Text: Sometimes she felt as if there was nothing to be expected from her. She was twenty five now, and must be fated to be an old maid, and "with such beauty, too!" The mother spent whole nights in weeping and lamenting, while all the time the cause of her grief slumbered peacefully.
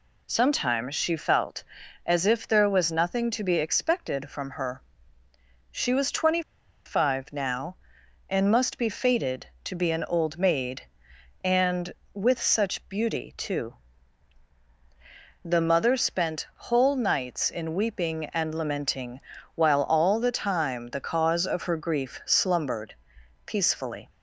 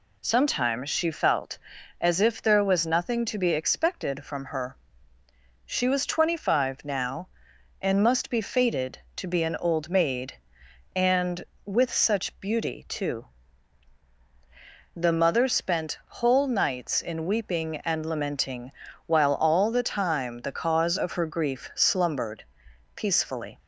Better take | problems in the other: second | pauses between "twenty" and "five"; at 6.4 s; 0.45 s long // pauses between "slumbered" and "peacefully"; noticeable; at 22.9 s; 0.52 s long; noticeable in the second

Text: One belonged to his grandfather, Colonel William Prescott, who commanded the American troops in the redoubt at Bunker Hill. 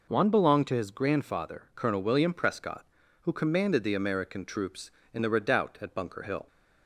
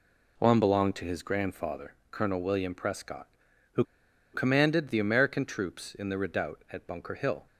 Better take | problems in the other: first | pauses between "who" and "commanded"; noticeable; at 3.8 s; 0.48 s long

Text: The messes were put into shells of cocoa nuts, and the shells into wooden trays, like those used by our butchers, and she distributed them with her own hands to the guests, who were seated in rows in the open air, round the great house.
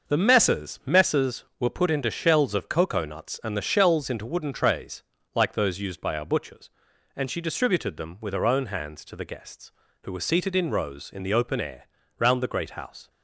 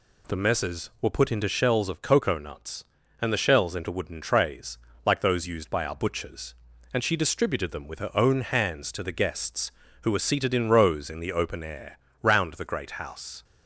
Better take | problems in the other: second | says "messes" twice; at 0.8 s

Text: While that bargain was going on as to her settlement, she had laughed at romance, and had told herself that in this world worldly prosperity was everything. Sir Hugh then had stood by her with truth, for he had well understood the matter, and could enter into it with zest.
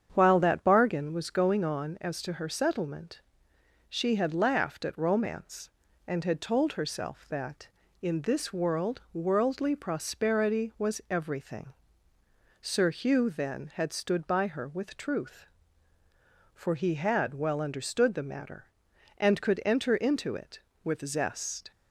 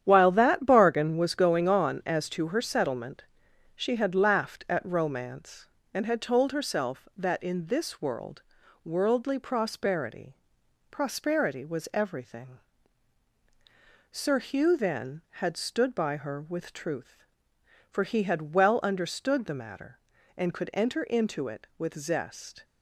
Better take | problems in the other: first | starts louder than the rest; strong; until 1.0 s; 9.5 dB; strong in the first // pauses between "world" and "worldly"; at 8.4 s; 0.42 s long // says "prosperity" twice; at 10.9 s

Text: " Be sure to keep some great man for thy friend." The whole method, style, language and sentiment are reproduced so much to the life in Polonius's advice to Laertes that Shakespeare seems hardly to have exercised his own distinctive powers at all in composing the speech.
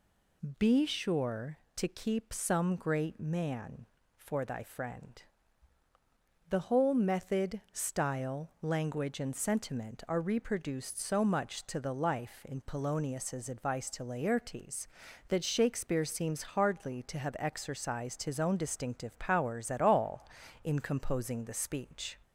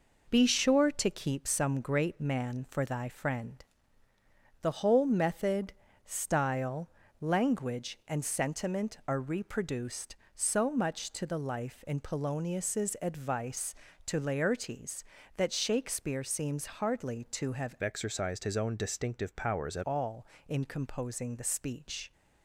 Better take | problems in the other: first | changes voice from "exercised" to "at"; from 17.8 to 19.8 s; 2.0 s long

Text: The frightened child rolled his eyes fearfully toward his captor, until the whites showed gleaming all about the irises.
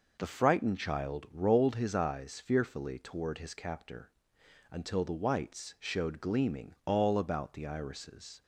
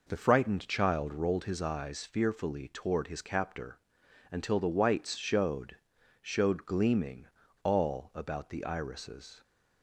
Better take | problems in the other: first | says "showed" twice; at 6.2 s // pauses between "gleaming" and "all"; at 7.2 s; 0.37 s long

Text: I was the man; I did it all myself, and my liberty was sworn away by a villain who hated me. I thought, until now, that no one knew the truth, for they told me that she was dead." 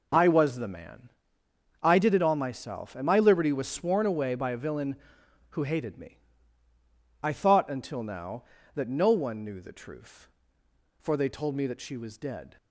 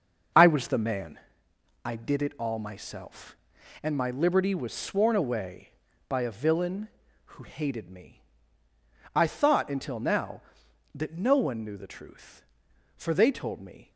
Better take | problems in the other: first | starts louder than the rest; until 2.0 s; 6 dB // stops before "that she was dead"; at 13.9 s

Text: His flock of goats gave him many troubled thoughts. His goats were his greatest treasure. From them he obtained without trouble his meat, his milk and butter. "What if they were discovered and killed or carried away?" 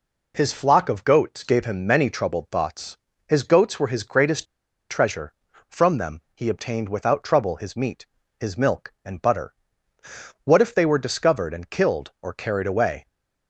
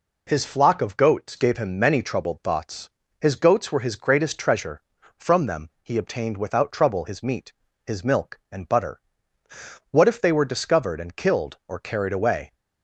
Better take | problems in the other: second | pauses between "greatest" and "treasure"; at 4.4 s; 0.44 s long

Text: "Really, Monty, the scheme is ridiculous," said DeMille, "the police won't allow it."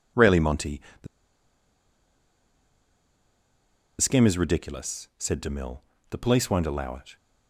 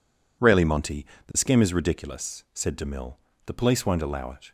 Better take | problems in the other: second | pauses between "the" and "scheme"; strong; at 1.0 s; 2.9 s long

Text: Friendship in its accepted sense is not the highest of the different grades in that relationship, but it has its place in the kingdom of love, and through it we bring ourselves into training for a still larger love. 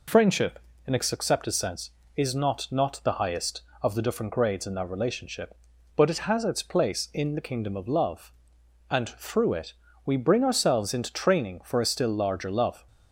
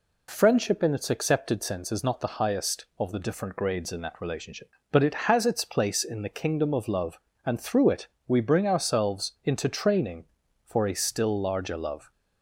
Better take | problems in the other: second | says "not" twice; at 2.7 s // pauses between "it" and "we"; slight; at 9.7 s; 0.32 s long; slight in the second

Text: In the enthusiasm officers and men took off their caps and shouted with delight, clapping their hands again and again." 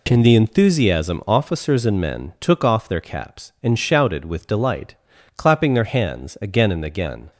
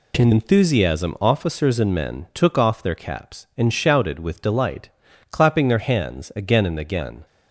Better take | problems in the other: first | skips "the"; at 0.3 s

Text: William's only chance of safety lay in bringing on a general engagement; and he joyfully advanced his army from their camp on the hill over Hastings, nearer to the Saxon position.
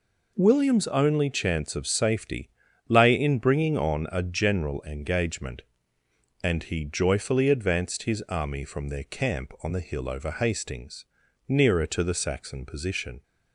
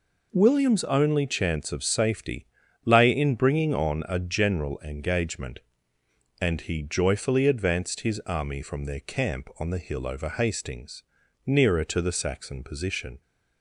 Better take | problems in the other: neither | pauses between "safety" and "lay"; the same in both

